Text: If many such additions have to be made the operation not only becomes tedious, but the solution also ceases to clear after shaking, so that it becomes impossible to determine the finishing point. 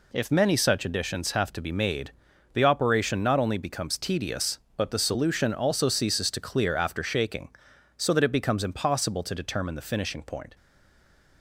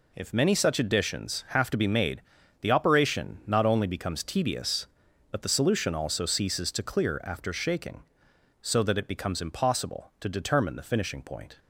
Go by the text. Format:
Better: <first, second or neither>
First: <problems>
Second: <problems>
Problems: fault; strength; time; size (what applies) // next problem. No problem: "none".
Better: second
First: pauses between "made" and "the"; at 2.1 s; 0.42 s long // stays silent after the last word; slight; from 10.5 s on; 0.9 s long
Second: pauses between "made" and "the"; at 2.2 s; 0.40 s long